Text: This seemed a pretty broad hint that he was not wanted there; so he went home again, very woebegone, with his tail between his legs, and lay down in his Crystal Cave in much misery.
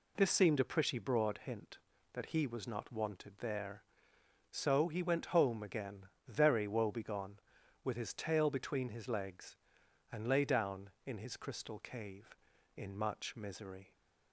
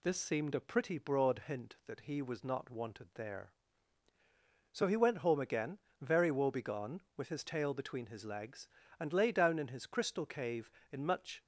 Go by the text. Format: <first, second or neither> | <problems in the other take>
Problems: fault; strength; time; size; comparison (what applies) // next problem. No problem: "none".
first | stops before "misery"; at 11.4 s